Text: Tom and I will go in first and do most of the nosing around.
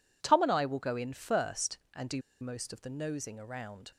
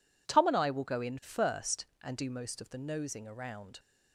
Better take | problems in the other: second | pauses between "do" and "most"; slight; at 2.2 s; 0.19 s long

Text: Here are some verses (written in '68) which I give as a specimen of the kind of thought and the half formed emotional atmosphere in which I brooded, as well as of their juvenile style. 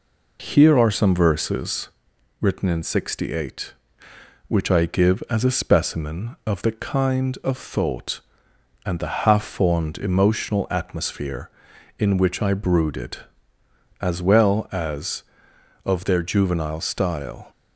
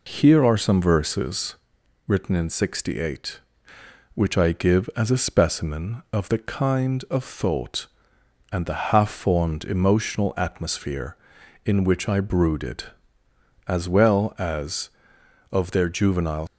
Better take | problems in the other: first | stops before "style"; at 16.4 s

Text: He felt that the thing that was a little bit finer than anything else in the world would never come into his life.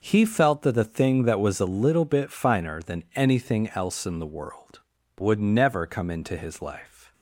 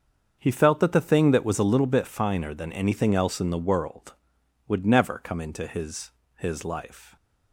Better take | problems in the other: first | starts louder than the rest; until 1.4 s; 7 dB // says "his" twice; at 6.3 s

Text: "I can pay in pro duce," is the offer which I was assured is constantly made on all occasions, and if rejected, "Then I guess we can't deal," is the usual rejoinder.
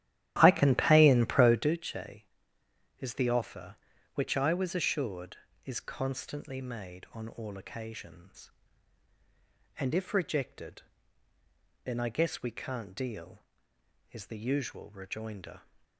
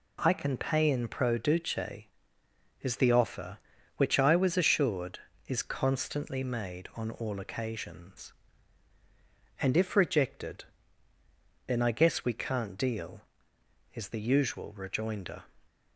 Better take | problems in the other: second | starts louder than the rest; strong; until 1.8 s; 13 dB

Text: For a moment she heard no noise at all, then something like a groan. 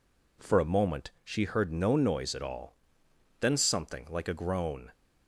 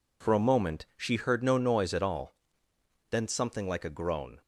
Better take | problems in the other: neither | none

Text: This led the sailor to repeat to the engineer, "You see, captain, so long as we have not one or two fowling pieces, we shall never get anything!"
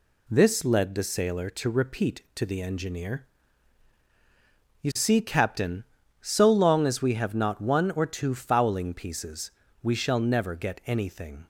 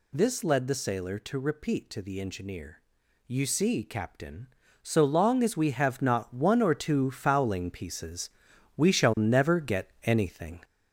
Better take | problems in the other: first | gets louder; noticeable; throughout; 4 dB

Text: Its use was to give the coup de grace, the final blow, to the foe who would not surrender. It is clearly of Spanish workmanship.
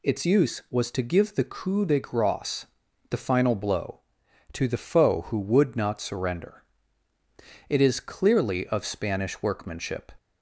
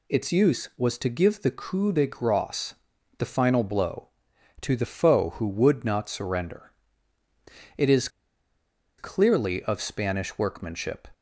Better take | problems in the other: first | pauses between "is" and "clearly"; noticeable; at 8.0 s; 0.90 s long

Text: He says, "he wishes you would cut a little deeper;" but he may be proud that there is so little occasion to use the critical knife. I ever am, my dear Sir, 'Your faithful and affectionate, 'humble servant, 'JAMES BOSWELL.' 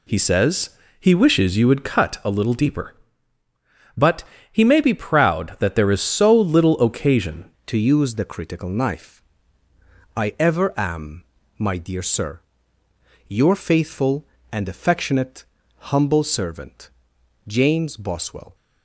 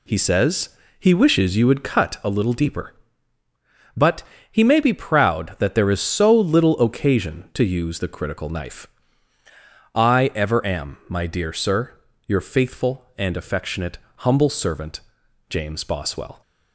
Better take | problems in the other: second | pauses between "but" and "he"; slight; at 4.2 s; 0.28 s long; slight in the second // changes voice at "to"; from 7.6 s on; 10.9 s long

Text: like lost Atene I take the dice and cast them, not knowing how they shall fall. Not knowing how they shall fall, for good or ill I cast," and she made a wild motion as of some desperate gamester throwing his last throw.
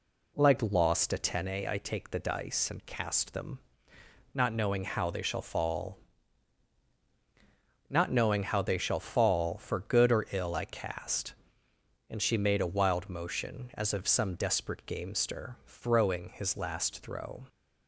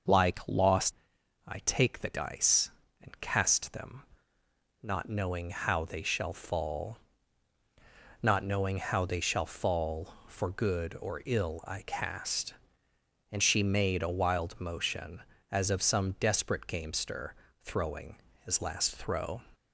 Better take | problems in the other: first | skips "Atene"; at 0.9 s // pauses between "gamester" and "throwing"; slight; at 17.3 s; 0.30 s long // pauses between "throwing" and "his"; slight; at 18.1 s; 0.28 s long

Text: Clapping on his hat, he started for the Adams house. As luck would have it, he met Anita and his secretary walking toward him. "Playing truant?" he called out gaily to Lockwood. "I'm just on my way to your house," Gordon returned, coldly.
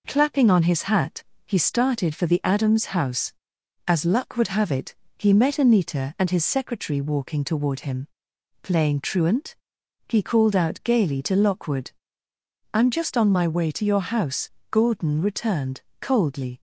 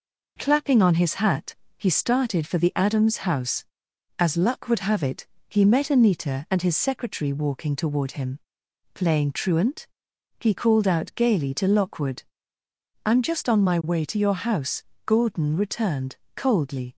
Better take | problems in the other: neither | none

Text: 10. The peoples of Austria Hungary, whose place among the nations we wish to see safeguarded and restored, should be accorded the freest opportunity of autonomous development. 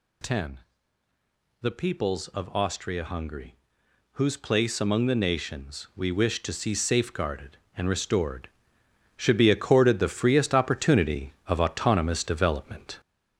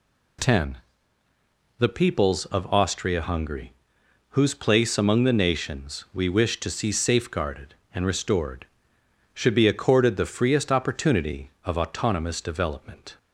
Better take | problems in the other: second | gets louder; noticeable; throughout; 5 dB

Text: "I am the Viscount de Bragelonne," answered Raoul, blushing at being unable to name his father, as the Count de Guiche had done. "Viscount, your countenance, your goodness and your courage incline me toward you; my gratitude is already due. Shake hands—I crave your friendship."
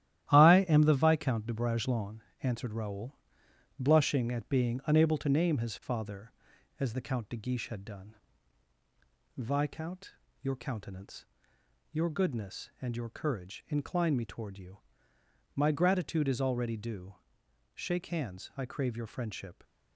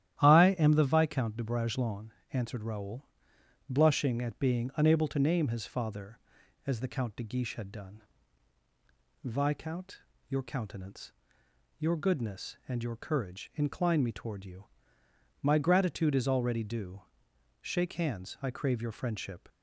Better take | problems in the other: second | gets quieter; strong; throughout; 7.5 dB // starts louder than the rest; strong; until 1.3 s; 12.5 dB; strong in the second

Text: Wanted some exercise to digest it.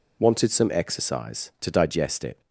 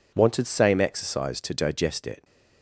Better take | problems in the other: first | says "same" for "some"; at 0.4 s

